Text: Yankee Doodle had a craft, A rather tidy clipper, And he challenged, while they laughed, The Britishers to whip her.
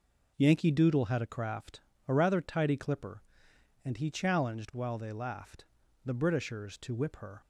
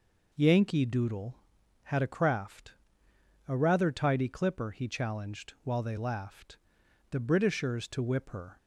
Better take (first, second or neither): first